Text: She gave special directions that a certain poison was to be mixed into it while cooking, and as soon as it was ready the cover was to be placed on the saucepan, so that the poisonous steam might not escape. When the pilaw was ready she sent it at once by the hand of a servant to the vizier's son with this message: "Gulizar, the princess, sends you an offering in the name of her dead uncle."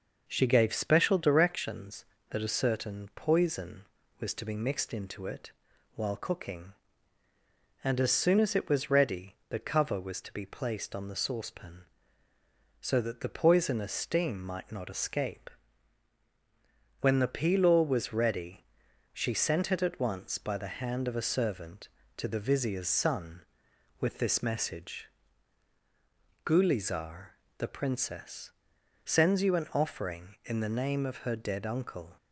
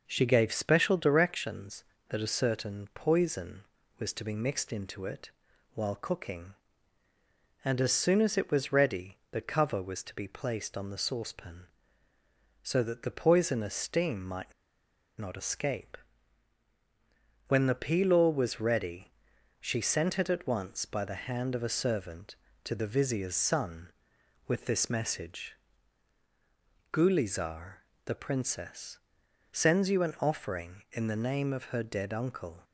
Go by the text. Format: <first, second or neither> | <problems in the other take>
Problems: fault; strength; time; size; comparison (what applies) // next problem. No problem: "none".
first | pauses between "it" and "while"; at 5.3 s; 0.44 s long; also in the first // pauses between "ready" and "the"; slight; at 9.1 s; 0.16 s long; slight in the first // pauses between "might" and "not"; noticeable; at 14.5 s; 0.67 s long // pauses between "ready" and "she"; noticeable; at 19.1 s; 0.48 s long; noticeable in the first